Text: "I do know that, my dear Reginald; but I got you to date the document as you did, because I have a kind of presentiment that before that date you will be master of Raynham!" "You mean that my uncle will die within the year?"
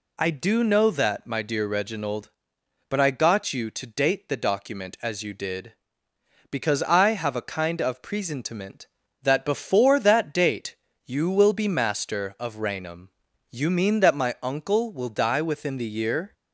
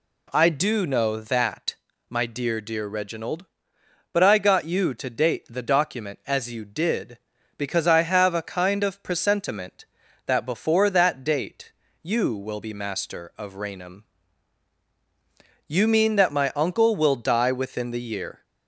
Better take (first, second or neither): first